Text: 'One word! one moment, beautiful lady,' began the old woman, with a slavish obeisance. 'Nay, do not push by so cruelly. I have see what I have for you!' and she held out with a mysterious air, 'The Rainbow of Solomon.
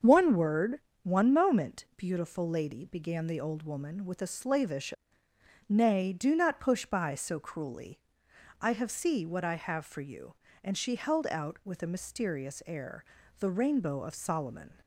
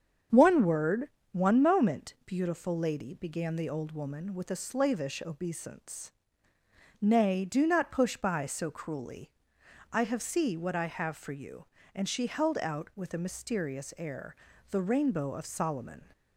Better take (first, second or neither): second